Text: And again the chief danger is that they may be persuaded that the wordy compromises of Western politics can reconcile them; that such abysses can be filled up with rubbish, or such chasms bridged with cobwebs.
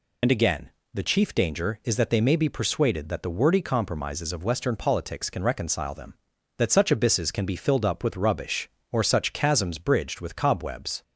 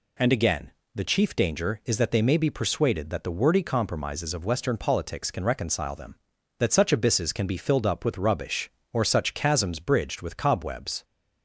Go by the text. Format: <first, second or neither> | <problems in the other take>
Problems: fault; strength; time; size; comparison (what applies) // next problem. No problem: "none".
second | loses the start of "And"; at 0.2 s; 65 ms // pauses between "again" and "the"; slight; at 0.7 s; 0.24 s long; slight in the second